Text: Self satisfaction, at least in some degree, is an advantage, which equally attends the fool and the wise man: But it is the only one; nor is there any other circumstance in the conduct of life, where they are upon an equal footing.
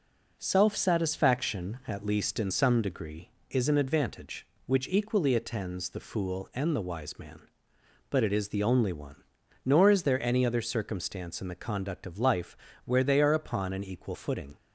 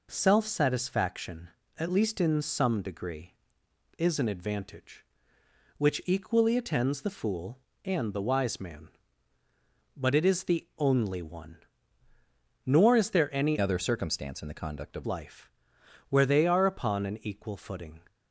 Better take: first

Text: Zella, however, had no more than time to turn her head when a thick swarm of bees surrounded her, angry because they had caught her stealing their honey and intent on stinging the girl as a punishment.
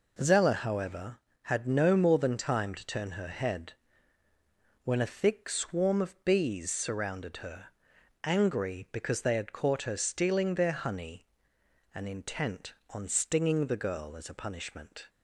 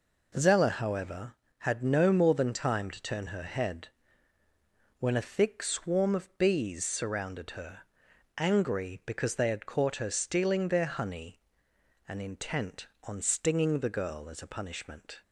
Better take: neither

